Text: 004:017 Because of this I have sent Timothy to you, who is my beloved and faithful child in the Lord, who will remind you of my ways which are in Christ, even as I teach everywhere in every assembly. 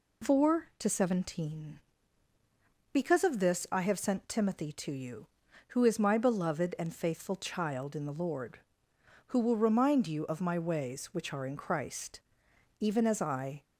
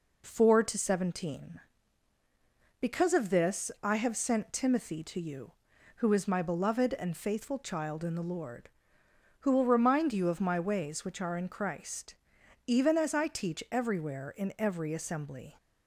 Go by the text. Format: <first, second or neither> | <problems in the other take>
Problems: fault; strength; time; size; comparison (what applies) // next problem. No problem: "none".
second | stops before "teach everywhere in every assembly"; at 13.6 s